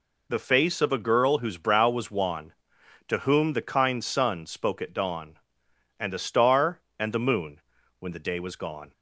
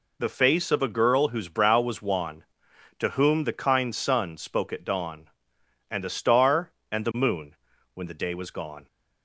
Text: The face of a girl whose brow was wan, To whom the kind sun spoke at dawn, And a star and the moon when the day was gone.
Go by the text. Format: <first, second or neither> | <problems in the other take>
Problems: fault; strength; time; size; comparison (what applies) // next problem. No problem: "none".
neither | pauses between "moon" and "when"; the same in both